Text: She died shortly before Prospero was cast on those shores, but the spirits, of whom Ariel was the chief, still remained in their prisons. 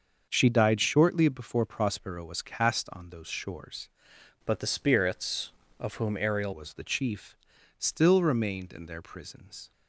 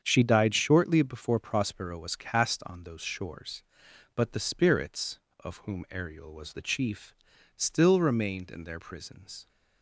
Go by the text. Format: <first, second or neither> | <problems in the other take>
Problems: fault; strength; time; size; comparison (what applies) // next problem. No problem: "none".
second | starts louder than the rest; until 1.3 s; 6.5 dB; strong in the second // changes voice from "but" to "Ariel"; from 4.4 to 6.5 s; 2.1 s long